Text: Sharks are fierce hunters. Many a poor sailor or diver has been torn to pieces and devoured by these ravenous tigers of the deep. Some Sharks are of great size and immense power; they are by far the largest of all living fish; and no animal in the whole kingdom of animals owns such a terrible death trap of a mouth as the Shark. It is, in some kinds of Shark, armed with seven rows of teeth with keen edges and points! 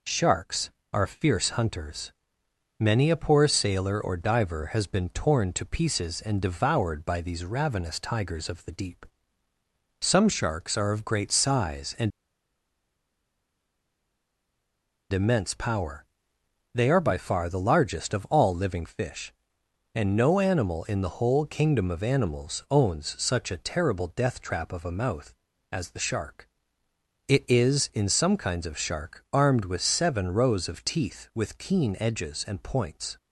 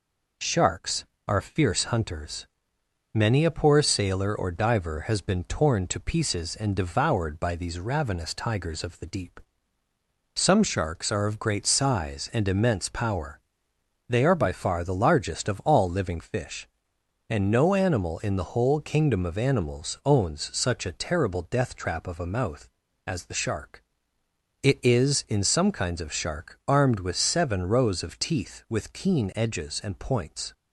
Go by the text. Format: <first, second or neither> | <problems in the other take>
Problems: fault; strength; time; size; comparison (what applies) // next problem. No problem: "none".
second | pauses between "and" and "immense"; strong; at 12.1 s; 3.0 s long